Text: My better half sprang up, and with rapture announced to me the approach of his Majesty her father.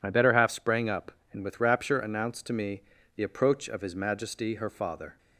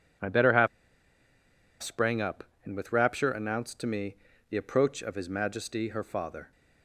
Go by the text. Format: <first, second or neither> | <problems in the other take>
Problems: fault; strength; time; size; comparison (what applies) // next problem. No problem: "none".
first | pauses between "half" and "sprang"; at 0.6 s; 1.1 s long // pauses between "me" and "the"; slight; at 4.1 s; 0.34 s long; slight in the first